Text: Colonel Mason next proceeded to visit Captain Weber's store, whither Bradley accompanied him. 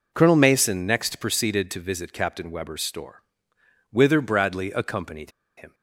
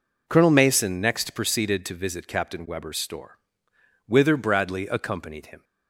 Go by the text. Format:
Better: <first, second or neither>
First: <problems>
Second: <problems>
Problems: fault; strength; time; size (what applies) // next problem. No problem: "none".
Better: second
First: pauses between "accompanied" and "him"; slight; at 5.3 s; 0.26 s long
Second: none